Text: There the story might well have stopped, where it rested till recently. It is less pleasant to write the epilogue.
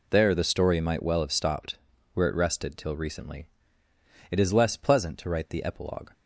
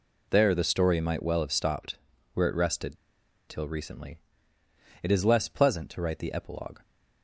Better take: first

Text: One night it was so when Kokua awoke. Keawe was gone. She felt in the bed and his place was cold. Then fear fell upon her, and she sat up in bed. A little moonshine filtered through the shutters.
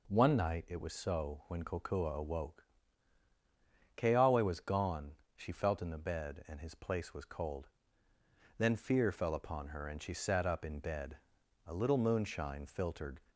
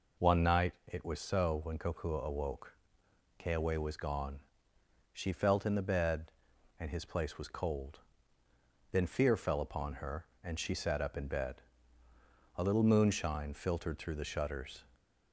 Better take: second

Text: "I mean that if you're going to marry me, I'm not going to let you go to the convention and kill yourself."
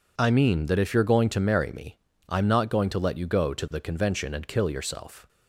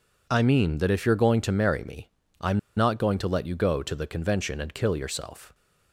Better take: first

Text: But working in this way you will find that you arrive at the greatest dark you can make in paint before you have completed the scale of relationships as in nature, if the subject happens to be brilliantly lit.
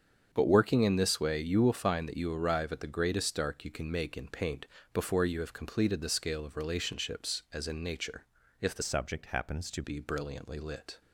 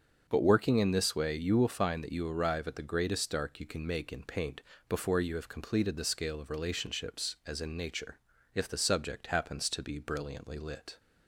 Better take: second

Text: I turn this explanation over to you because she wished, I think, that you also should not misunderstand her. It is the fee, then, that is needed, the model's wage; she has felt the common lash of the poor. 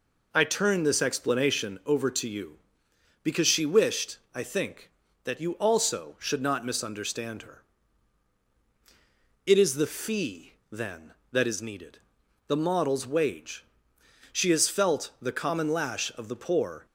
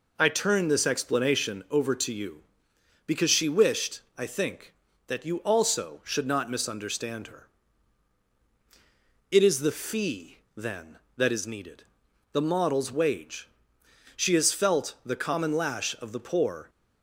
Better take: neither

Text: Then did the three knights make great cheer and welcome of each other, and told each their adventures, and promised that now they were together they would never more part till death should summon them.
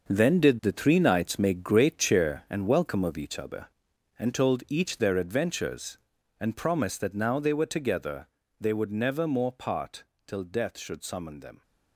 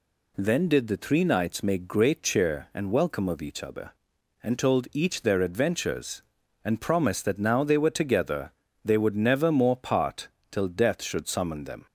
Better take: second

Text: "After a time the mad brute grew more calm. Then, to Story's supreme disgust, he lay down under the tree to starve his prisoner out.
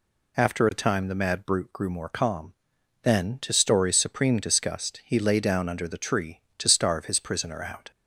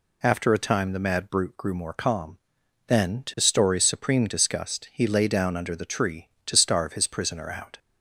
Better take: neither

